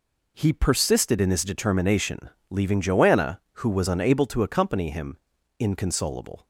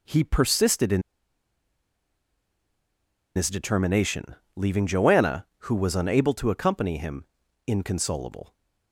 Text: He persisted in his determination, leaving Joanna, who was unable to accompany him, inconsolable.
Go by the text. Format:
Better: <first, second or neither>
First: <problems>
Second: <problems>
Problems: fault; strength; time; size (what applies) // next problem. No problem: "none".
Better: first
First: none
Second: pauses between "in" and "his"; strong; at 1.0 s; 2.3 s long